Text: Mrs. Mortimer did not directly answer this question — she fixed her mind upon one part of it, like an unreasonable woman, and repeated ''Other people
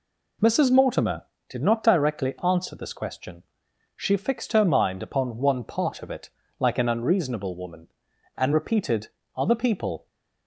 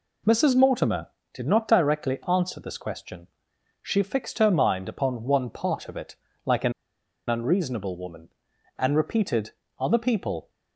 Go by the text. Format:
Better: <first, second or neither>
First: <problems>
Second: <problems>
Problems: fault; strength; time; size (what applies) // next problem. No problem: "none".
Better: first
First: pauses between "repeated" and "Other"; slight; at 9.0 s; 0.26 s long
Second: pauses between "an" and "unreasonable"; noticeable; at 6.7 s; 0.55 s long // pauses between "repeated" and "Other"; slight; at 9.5 s; 0.26 s long